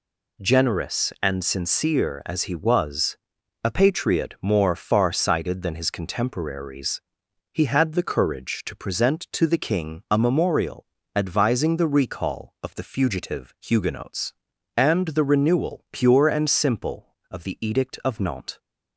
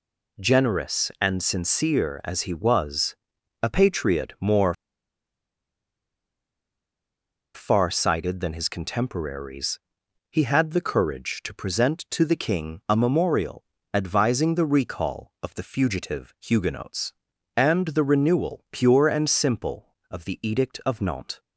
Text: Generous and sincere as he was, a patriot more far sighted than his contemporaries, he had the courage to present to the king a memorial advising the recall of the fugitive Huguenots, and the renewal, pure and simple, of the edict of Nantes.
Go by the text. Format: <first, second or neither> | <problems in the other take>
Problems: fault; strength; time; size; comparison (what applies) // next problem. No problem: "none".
first | pauses between "more" and "far"; strong; at 4.7 s; 2.8 s long // pauses between "memorial" and "advising"; slight; at 13.6 s; 0.30 s long; slight in the first